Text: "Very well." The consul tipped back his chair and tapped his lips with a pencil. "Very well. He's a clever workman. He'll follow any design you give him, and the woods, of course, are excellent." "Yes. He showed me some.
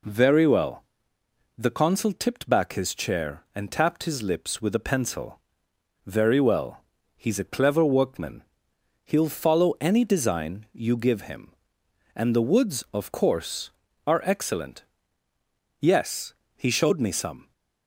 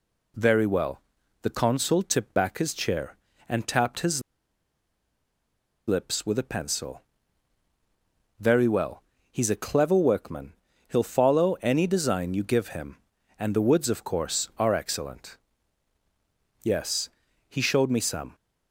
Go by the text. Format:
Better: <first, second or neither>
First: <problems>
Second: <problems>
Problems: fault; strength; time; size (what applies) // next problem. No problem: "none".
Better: first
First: none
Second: pauses between "his" and "lips"; strong; at 4.2 s; 1.6 s long